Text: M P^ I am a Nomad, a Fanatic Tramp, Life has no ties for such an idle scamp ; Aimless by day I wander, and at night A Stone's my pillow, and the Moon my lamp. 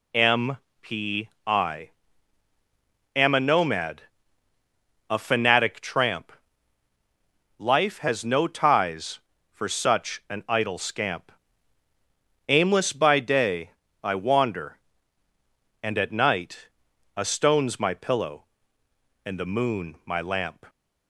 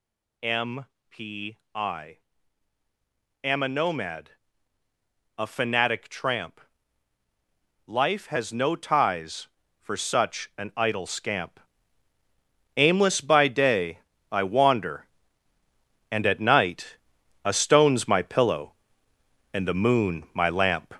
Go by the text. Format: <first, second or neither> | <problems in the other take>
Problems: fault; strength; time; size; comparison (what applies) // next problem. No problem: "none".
first | gets louder; noticeable; throughout; 5 dB // pauses between "M" and "P"; slight; at 0.8 s; 0.24 s long; slight in the first // pauses between "P" and "I"; slight; at 1.5 s; 0.18 s long; slight in the first // pauses between "I" and "am"; at 2.1 s; 1.2 s long; also in the first // pauses between "day" and "I"; slight; at 13.9 s; 0.30 s long; slight in the first // pauses between "night" and "A"; noticeable; at 16.9 s; 0.48 s long; noticeable in the first